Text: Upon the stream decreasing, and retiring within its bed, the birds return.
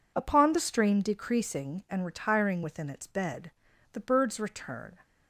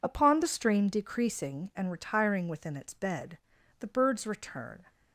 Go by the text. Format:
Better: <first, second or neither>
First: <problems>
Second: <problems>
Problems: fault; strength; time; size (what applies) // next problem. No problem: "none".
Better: neither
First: none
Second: none